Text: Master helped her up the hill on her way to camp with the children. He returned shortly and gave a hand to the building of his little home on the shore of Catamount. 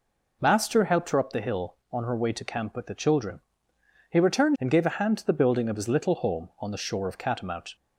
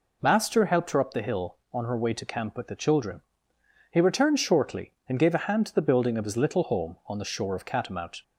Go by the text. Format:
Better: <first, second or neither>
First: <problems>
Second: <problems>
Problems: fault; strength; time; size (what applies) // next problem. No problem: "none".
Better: second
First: skips "shortly"; at 4.5 s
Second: none